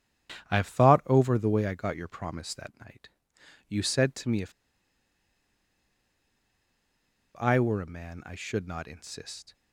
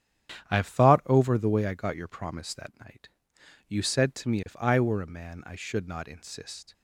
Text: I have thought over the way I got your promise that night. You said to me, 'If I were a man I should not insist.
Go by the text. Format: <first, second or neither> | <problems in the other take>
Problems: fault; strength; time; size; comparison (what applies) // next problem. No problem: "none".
second | starts louder than the rest; strong; until 1.5 s; 10 dB; strong in the second // pauses between "If" and "I"; strong; at 4.5 s; 2.8 s long